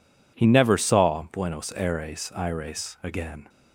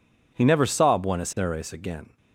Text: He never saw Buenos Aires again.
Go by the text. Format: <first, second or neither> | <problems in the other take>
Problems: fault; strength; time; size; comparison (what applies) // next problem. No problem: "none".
second | says "Aires" twice; at 2.3 s